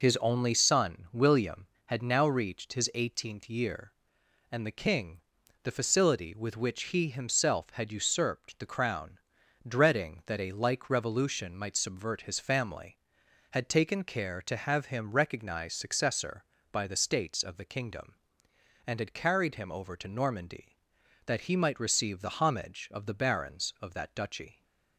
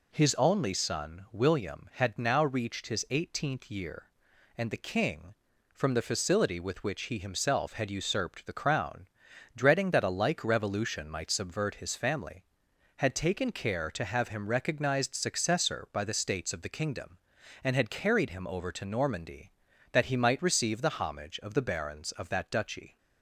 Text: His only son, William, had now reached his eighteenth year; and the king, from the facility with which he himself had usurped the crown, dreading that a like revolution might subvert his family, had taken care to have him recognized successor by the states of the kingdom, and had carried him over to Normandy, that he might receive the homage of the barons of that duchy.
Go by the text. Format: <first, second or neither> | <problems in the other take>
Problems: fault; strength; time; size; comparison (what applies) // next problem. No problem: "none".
second | skips "from"; at 5.4 s